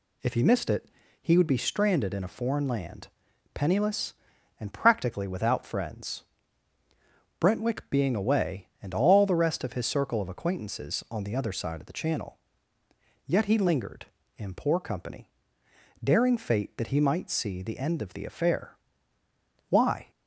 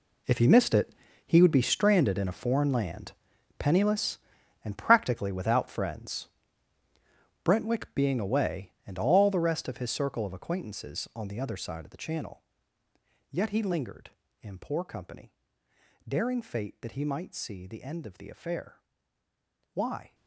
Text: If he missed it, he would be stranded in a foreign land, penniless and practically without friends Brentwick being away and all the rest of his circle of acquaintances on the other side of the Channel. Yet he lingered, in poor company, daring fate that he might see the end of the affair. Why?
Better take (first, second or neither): first